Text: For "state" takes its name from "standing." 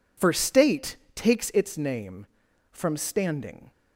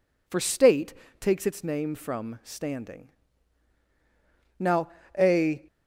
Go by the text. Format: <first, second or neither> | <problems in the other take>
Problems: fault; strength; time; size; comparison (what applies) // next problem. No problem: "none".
first | pauses between "state" and "takes"; slight; at 0.9 s; 0.28 s long; slight in the first // goes on to say "Now a"; noticeable; from 4.5 s on; 1.0 s long